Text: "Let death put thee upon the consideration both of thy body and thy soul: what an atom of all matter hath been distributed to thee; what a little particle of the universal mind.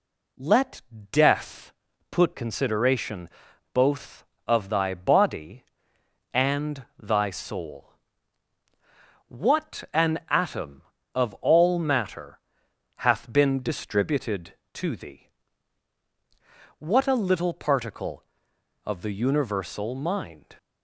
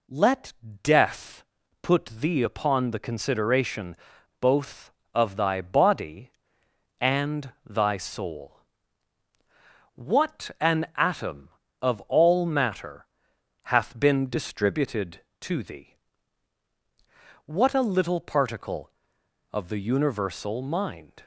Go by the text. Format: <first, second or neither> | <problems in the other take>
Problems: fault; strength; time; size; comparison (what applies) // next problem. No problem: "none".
second | pauses between "Let" and "death"; slight; at 0.8 s; 0.30 s long; slight in the second // pauses between "death" and "put"; at 1.7 s; 0.38 s long; also in the second // skips "thee upon the"; at 2.3 s // pauses between "consideration" and "both"; noticeable; at 3.2 s; 0.46 s long; noticeable in the second // pauses between "matter" and "hath"; noticeable; at 12.3 s; 0.60 s long; noticeable in the second